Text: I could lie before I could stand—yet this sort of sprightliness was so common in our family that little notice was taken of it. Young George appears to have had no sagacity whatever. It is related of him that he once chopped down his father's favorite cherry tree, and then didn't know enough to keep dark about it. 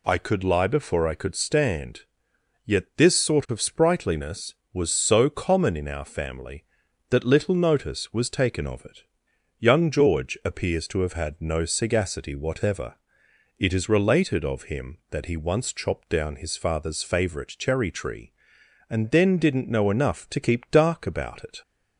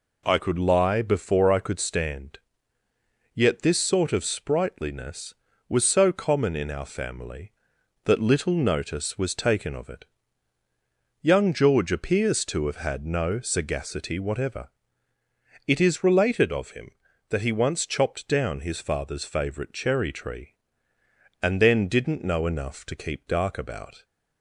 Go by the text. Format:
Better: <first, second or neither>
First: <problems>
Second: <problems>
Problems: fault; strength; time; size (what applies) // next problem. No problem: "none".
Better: first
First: none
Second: stops before "it"; at 24.0 s